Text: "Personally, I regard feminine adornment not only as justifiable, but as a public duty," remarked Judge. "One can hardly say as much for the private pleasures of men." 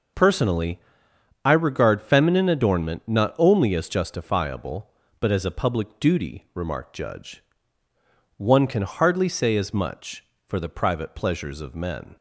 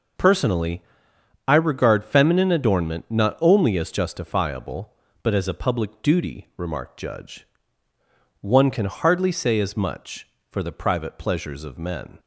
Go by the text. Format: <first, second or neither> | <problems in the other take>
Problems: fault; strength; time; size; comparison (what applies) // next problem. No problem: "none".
neither | none